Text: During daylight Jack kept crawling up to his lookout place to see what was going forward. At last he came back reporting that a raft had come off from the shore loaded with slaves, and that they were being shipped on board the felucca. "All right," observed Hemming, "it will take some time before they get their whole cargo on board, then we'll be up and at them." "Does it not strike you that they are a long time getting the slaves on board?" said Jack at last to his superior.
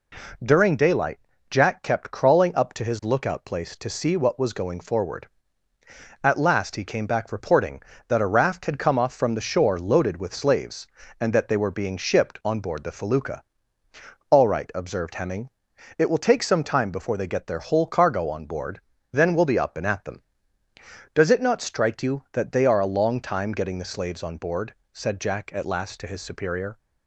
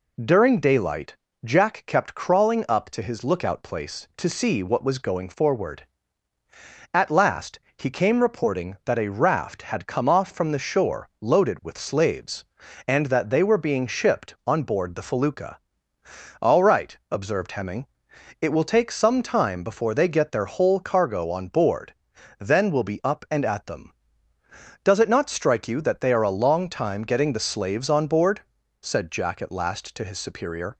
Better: first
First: pauses between "daylight" and "Jack"; slight; at 1.1 s; 0.30 s long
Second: pauses between "daylight" and "Jack"; slight; at 1.1 s; 0.28 s long // pauses between "last" and "he"; slight; at 7.5 s; 0.18 s long // skips "back"; at 8.2 s

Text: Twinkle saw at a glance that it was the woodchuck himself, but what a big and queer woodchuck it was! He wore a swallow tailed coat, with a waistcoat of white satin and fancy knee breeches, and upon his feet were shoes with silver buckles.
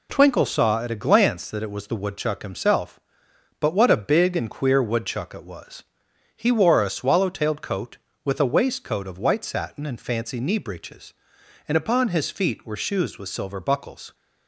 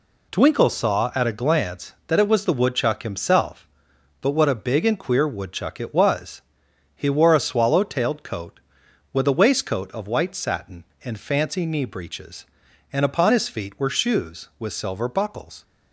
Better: neither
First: none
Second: none

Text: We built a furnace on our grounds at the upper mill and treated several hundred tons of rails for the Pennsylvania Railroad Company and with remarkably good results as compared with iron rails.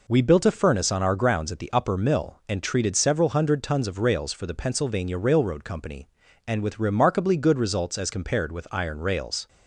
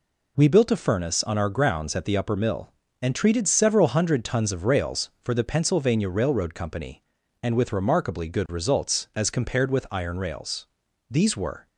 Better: first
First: none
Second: goes on to say "These were"; from 11.0 s on; 0.58 s long

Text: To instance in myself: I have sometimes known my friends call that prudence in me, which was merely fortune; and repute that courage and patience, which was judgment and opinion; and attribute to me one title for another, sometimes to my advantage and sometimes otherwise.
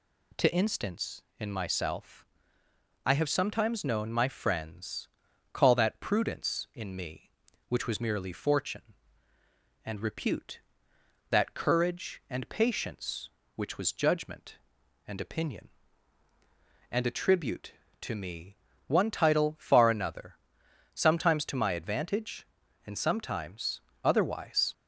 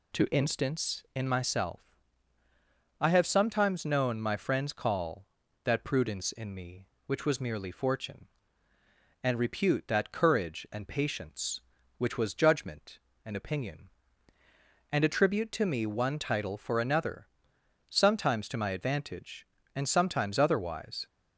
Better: second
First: pauses between "friends" and "call"; noticeable; at 5.0 s; 0.46 s long // pauses between "me" and "one"; slight; at 18.5 s; 0.30 s long // says "far" for "for"; at 19.5 s // pauses between "sometimes" and "otherwise"; slight; at 23.8 s; 0.20 s long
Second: none

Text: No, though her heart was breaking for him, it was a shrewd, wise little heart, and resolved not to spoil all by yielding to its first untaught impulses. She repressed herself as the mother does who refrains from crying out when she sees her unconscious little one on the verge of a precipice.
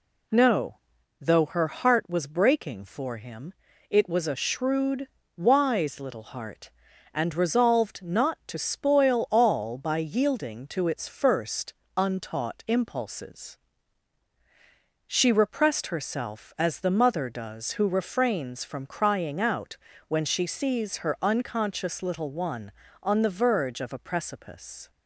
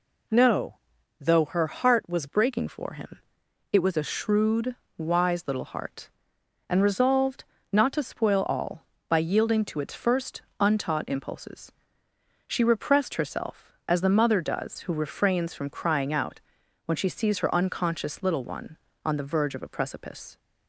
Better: first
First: pauses between "first" and "untaught"; slight; at 11.7 s; 0.24 s long // pauses between "out" and "when"; slight; at 19.7 s; 0.32 s long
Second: changes voice at "breaking"; from 2.2 s on; 18.1 s long // pauses between "resolved" and "not"; slight; at 7.4 s; 0.28 s long // pauses between "first" and "untaught"; slight; at 10.4 s; 0.18 s long // pauses between "out" and "when"; noticeable; at 16.3 s; 0.46 s long

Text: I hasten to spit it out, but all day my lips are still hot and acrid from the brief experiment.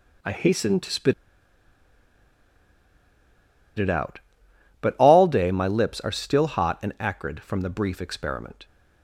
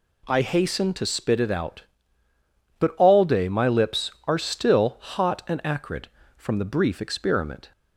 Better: second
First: pauses between "spit" and "it"; strong; at 1.1 s; 2.6 s long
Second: none

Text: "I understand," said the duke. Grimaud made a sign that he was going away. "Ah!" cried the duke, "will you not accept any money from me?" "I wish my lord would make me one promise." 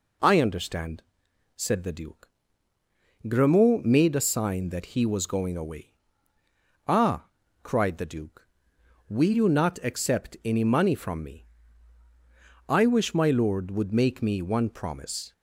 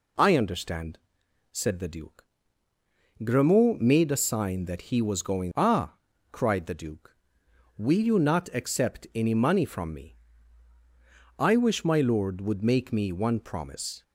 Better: first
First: none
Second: skips "away"; at 5.5 s

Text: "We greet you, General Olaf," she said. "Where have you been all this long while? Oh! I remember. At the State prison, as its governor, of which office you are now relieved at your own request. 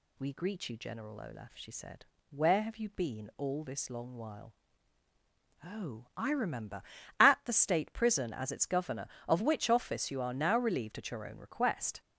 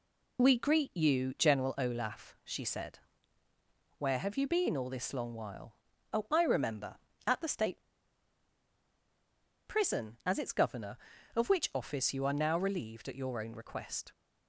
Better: first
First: none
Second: pauses between "State" and "prison"; strong; at 7.8 s; 1.8 s long

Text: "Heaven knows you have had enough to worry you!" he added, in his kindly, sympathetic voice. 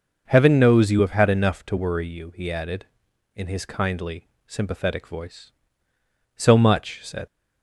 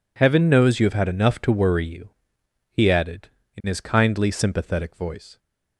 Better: second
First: goes on to say "So much said"; noticeable; from 6.3 s on; 0.90 s long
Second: none

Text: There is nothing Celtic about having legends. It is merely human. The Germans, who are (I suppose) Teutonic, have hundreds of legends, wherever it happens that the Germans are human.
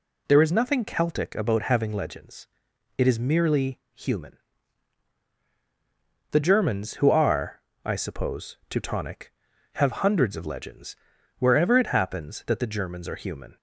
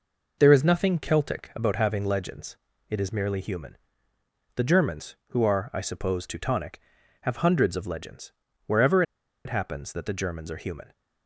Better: first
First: none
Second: pauses between "wherever" and "it"; at 9.0 s; 0.43 s long

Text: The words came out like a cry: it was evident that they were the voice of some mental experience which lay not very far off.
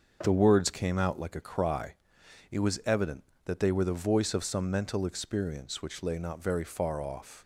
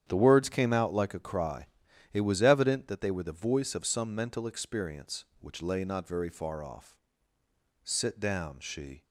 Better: first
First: starts louder than the rest; until 1.2 s; 6.5 dB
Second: starts louder than the rest; strong; until 1.0 s; 9 dB // goes on to say "Sit down she"; noticeable; from 7.8 s on; 1.2 s long

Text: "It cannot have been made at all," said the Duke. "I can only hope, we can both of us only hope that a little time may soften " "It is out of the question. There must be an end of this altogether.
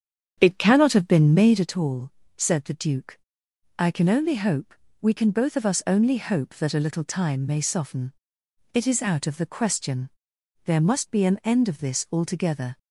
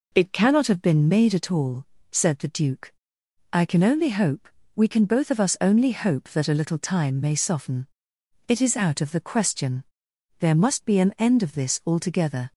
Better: second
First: starts louder than the rest; strong; until 1.7 s; 8 dB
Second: none

